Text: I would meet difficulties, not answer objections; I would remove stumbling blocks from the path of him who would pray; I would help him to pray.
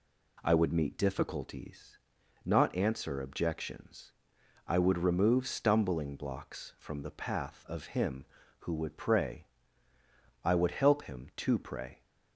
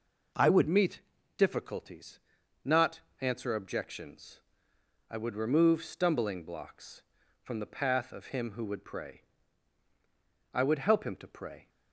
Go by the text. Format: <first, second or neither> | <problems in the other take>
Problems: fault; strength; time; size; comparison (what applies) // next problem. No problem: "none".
first | changes voice at "meet"; from 0.6 s on; 11.0 s long // pauses between "meet" and "difficulties"; at 1.0 s; 0.38 s long // pauses between "not" and "answer"; slight; at 3.0 s; 0.18 s long